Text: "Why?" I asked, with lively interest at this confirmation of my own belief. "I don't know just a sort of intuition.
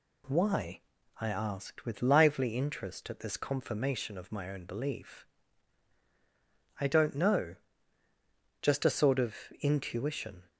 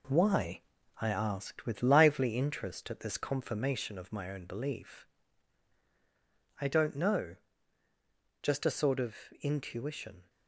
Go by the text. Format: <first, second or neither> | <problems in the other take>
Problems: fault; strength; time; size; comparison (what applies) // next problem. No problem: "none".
first | gets quieter; noticeable; throughout; 4.5 dB // pauses between "know" and "just"; at 7.3 s; 1.0 s long; also in the first // pauses between "of" and "intuition"; slight; at 9.1 s; 0.26 s long; slight in the first